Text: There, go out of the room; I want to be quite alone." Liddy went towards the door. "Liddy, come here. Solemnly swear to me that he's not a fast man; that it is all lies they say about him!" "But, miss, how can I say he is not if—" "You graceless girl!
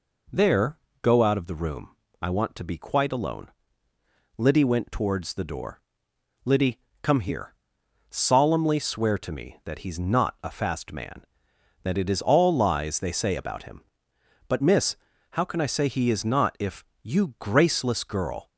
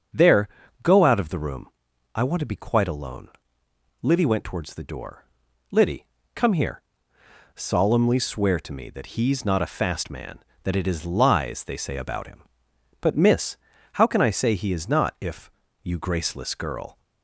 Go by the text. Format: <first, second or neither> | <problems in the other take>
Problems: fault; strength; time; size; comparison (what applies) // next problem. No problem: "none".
first | starts louder than the rest; until 1.4 s; 6.5 dB // skips "all"; at 11.0 s